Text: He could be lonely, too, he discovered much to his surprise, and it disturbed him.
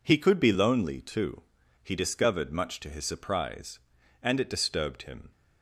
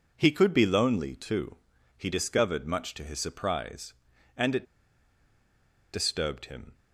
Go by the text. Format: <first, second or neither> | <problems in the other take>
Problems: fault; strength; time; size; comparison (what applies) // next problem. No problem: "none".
first | pauses between "it" and "disturbed"; strong; at 4.6 s; 1.2 s long